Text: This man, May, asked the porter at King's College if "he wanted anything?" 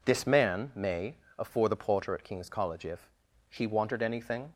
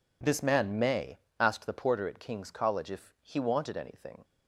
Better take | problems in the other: second | says "afore" for "asked"; at 1.3 s // pauses between "if" and "he"; at 3.0 s; 0.44 s long

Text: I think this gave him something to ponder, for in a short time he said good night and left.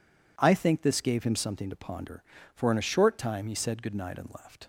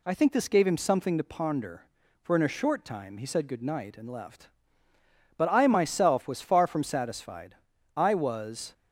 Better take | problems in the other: first | goes on to say "But I myself was far from satisfied I was"; strong; from 5.3 s on; 3.3 s long

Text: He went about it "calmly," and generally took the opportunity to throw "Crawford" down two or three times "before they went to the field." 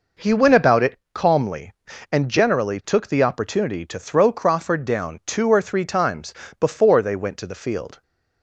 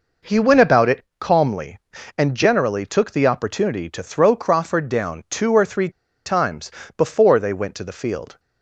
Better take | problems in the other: first | pauses between "it" and "calmly"; slight; at 1.0 s; 0.16 s long; slight in the first // pauses between "three" and "times"; slight; at 5.8 s; 0.36 s long // pauses between "times" and "before"; slight; at 6.7 s; 0.26 s long; slight in the first

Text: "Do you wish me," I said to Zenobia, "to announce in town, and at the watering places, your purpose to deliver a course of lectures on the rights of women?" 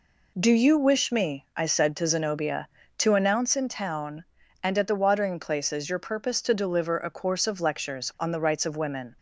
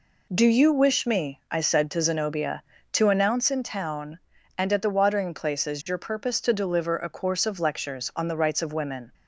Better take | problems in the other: neither | none

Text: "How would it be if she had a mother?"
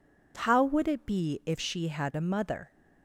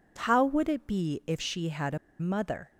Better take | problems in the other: first | pauses between "a" and "mother"; slight; at 1.9 s; 0.22 s long

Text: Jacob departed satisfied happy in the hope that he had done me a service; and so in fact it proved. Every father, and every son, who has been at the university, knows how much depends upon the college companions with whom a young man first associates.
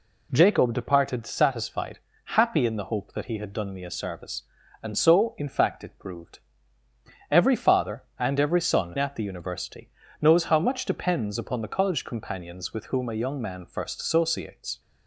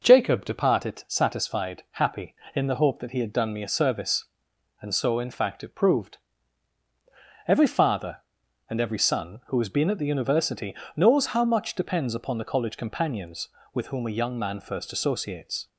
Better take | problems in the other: second | pauses between "satisfied" and "happy"; at 1.9 s; 0.38 s long // skips "who has been"; at 8.9 s

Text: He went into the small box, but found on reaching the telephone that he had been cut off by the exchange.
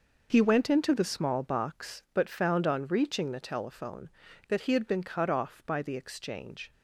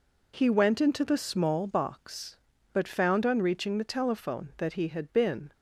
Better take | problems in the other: first | stops before "cut off by the exchange"; at 5.5 s

